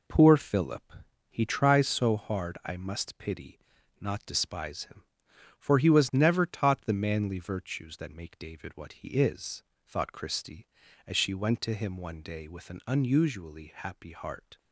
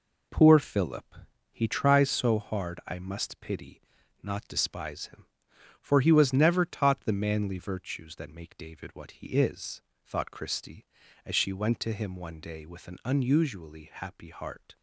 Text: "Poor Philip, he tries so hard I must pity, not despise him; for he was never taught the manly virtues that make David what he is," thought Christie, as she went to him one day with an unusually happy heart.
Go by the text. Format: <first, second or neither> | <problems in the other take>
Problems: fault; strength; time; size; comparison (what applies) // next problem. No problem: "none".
neither | none